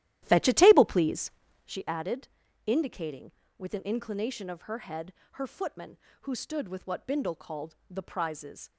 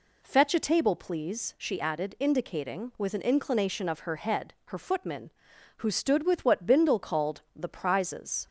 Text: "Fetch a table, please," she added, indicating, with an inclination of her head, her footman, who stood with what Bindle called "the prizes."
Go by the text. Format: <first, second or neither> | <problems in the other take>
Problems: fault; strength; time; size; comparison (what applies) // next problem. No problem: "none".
second | starts louder than the rest; strong; until 1.9 s; 13 dB // pauses between "called" and "the"; slight; at 7.7 s; 0.16 s long